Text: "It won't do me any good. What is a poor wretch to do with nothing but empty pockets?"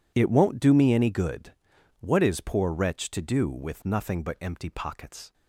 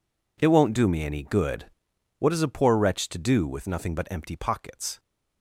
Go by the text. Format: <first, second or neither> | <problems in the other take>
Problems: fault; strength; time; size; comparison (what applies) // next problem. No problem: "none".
second | skips "a"; at 2.3 s